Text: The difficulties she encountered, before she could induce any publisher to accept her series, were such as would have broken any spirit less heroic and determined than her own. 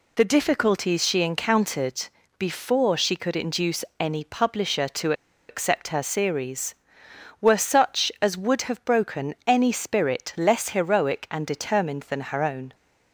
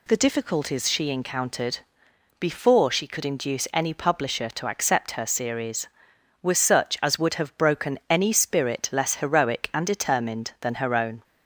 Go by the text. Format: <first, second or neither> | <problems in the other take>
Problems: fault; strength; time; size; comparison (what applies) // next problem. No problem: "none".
second | pauses between "to" and "accept"; slight; at 5.1 s; 0.36 s long